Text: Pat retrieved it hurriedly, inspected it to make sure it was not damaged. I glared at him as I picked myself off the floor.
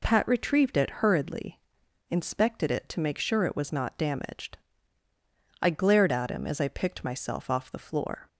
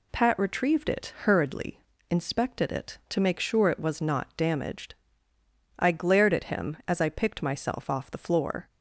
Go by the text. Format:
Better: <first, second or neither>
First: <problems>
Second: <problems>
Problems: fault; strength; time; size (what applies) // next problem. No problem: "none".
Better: neither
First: none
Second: none